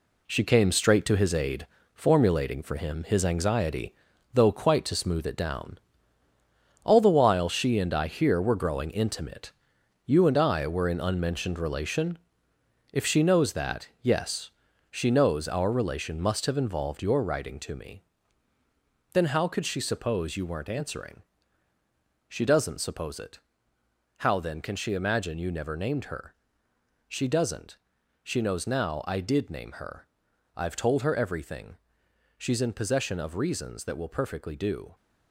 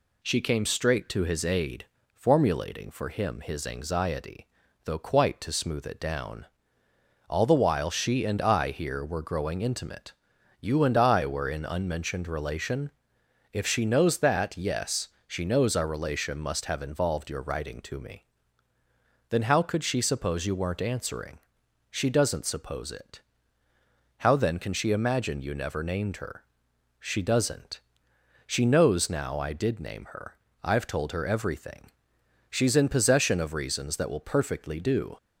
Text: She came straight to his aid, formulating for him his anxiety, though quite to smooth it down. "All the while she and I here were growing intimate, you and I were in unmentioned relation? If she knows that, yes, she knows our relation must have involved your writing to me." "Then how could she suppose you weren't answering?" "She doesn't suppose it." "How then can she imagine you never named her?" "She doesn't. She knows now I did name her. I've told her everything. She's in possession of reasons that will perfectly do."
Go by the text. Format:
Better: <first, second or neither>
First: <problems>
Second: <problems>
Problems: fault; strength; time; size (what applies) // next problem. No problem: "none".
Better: second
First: gets quieter; strong; throughout; 7.5 dB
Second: none